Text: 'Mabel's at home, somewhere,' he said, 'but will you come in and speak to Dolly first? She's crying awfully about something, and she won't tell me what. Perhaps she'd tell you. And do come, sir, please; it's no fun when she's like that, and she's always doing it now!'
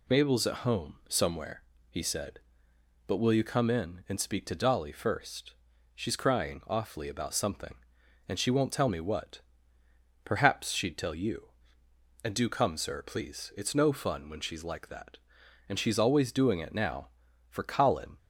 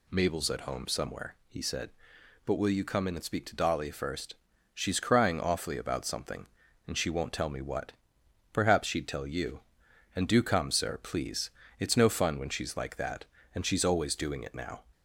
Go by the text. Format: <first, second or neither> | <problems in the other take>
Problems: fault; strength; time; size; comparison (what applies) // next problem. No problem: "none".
second | goes on to say "For Colin"; noticeable; from 17.4 s on; 0.68 s long